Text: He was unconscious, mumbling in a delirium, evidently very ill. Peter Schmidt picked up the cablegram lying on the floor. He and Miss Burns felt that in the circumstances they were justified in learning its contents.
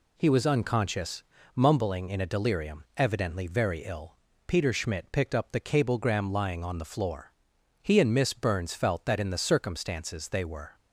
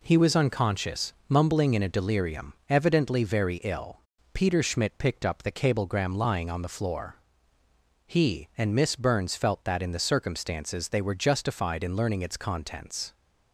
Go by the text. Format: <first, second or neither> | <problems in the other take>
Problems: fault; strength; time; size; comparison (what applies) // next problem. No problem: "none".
second | stops before "justified in learning its contents"; at 10.7 s